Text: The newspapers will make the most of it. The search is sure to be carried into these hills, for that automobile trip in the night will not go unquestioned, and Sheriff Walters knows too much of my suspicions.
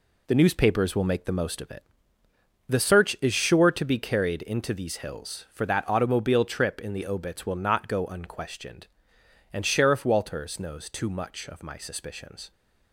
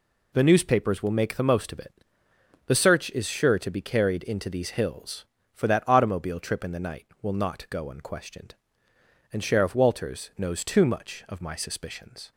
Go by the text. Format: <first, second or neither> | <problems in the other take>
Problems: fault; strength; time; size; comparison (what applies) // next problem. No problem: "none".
second | says "obits" for "night"; at 7.0 s